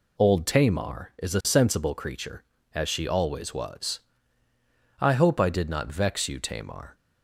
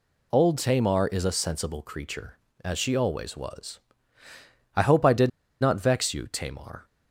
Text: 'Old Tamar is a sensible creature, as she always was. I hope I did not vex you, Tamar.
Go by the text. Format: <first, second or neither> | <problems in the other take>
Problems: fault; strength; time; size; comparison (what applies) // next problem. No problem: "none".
first | pauses between "did" and "not"; slight; at 5.2 s; 0.32 s long